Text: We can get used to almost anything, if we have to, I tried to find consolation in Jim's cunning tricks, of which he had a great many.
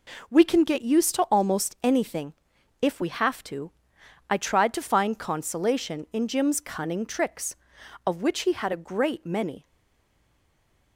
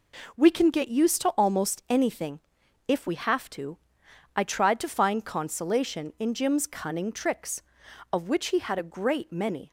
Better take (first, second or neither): second